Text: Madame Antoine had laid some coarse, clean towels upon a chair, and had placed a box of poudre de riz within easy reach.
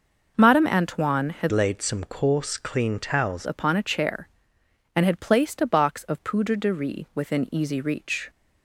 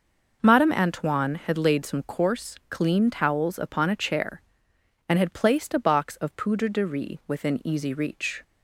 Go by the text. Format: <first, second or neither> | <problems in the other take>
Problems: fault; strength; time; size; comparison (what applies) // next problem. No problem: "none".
second | changes voice from "laid" to "towels"; from 1.5 to 3.4 s; 1.9 s long